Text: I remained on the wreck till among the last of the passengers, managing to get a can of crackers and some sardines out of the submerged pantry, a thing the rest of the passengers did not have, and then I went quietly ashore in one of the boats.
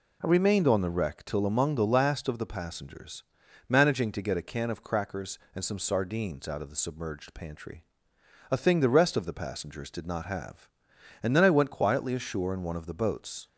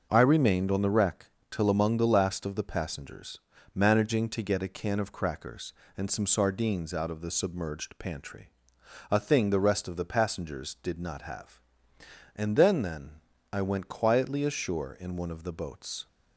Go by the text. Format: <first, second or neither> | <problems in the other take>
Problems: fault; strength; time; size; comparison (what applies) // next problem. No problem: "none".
first | starts louder than the rest; until 1.1 s; 6 dB // pauses between "wreck" and "till"; slight; at 1.2 s; 0.24 s long // says "then" twice; at 12.8 s